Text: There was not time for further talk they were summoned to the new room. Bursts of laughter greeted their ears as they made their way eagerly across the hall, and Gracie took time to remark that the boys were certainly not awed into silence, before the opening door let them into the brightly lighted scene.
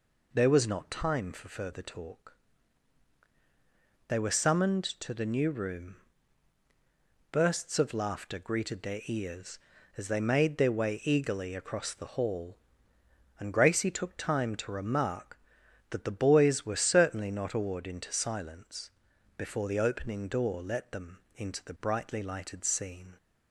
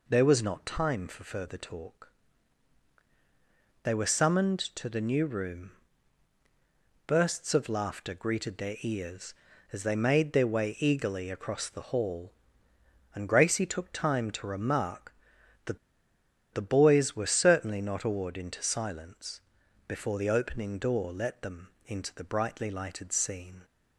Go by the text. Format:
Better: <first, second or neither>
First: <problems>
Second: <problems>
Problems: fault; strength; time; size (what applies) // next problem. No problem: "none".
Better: first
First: pauses between "talk" and "they"; strong; at 2.3 s; 1.7 s long // pauses between "them" and "into"; slight; at 21.2 s; 0.16 s long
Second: pauses between "talk" and "they"; strong; at 2.1 s; 1.7 s long // pauses between "that" and "the"; noticeable; at 15.7 s; 0.75 s long // pauses between "them" and "into"; slight; at 21.7 s; 0.16 s long